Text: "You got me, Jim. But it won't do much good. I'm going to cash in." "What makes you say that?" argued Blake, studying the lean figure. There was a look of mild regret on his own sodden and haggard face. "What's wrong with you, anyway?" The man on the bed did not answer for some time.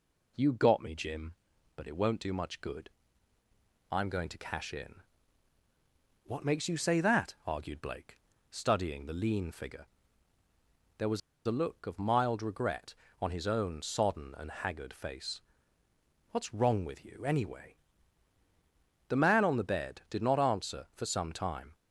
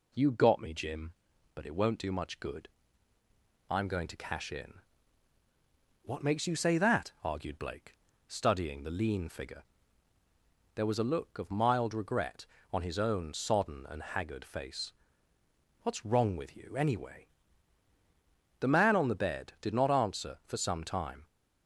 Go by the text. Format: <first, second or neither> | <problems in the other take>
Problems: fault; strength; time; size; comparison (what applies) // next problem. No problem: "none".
second | pauses between "was" and "a"; slight; at 11.2 s; 0.26 s long